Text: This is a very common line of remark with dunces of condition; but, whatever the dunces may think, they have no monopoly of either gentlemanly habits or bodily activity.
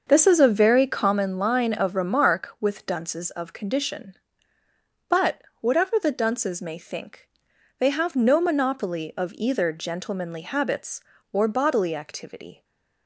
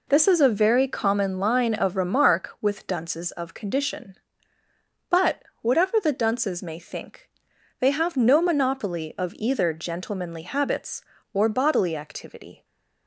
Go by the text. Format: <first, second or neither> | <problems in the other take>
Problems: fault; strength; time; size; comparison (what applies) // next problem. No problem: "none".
second | starts louder than the rest; until 1.2 s; 6 dB // stays silent after the last word; slight; from 12.5 s on; 0.5 s long